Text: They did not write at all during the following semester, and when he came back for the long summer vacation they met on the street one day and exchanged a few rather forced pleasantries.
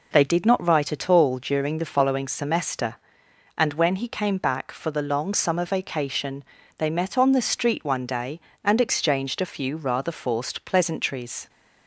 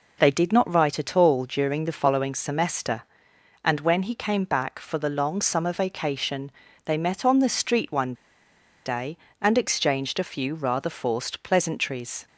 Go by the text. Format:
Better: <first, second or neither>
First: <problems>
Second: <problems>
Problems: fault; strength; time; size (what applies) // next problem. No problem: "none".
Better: first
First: pauses between "vacation" and "they"; slight; at 6.4 s; 0.34 s long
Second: pauses between "vacation" and "they"; slight; at 6.5 s; 0.34 s long // pauses between "one" and "day"; noticeable; at 8.1 s; 0.72 s long